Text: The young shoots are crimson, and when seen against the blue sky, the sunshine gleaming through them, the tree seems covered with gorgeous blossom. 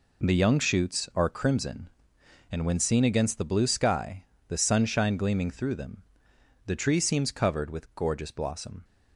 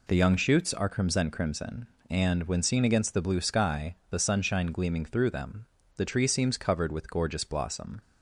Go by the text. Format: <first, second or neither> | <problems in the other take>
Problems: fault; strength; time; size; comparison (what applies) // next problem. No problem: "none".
first | says "crimson" twice; at 1.2 s